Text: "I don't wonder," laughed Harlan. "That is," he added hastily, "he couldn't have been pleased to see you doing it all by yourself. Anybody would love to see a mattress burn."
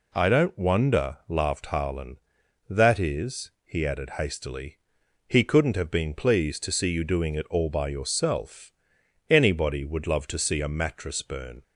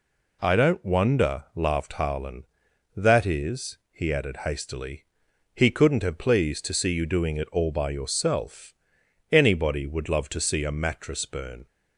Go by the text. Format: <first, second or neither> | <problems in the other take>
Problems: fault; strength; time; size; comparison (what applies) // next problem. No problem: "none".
first | skips "been"; at 6.1 s